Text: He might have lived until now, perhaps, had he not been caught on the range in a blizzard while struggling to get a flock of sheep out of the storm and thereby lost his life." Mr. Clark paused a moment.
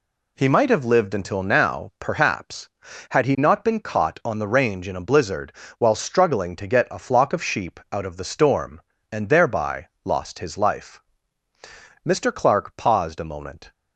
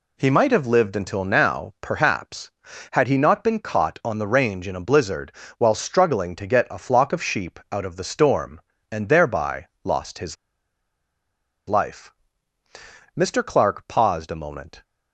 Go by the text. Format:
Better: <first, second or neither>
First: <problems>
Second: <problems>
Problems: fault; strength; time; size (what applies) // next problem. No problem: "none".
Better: first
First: pauses between "blizzard" and "while"; slight; at 5.5 s; 0.28 s long // pauses between "thereby" and "lost"; slight; at 9.8 s; 0.18 s long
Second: pauses between "blizzard" and "while"; slight; at 5.3 s; 0.28 s long // pauses between "thereby" and "lost"; slight; at 9.6 s; 0.18 s long // pauses between "his" and "life"; strong; at 10.3 s; 1.3 s long